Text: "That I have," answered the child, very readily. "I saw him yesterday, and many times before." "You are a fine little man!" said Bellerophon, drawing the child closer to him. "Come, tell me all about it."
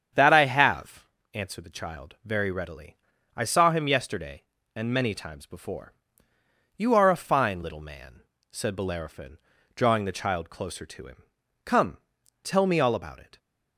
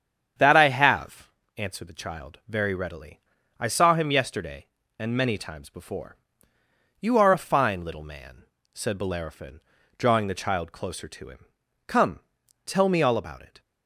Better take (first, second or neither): neither